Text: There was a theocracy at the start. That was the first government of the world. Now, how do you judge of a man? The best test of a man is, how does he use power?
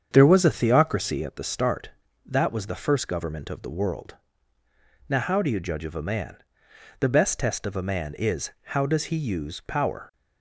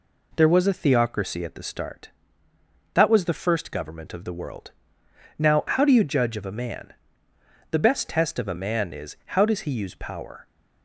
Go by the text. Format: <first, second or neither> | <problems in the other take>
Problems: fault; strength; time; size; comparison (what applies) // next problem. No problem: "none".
second | starts louder than the rest; strong; until 1.4 s; 7.5 dB